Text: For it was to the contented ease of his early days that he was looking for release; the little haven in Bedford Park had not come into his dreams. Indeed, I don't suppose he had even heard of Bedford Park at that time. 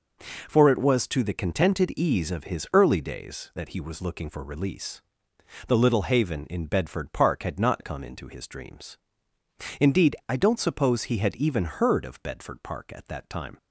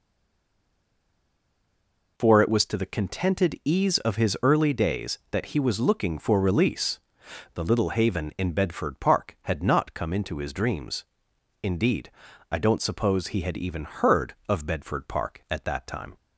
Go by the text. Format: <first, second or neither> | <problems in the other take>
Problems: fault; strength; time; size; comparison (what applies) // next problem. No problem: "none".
first | stays silent before the first word; until 2.1 s; 2.1 s long